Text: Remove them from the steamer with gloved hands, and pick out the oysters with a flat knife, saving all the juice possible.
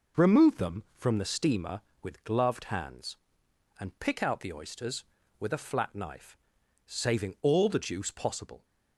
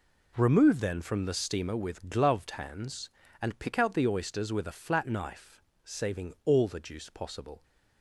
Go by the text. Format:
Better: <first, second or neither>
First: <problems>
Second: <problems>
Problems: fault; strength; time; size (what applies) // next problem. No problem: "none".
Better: first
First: none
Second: says "then" for "them"; at 0.7 s